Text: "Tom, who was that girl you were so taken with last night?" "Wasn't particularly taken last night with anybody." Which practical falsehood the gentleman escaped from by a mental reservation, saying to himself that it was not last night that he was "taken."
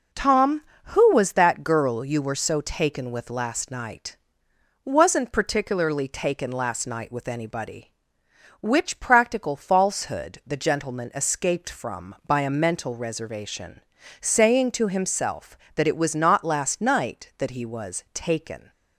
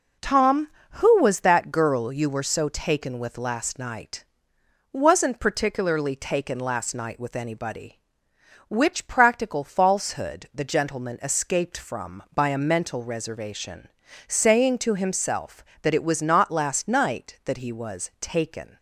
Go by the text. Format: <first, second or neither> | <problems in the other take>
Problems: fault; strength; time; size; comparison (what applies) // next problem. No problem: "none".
neither | none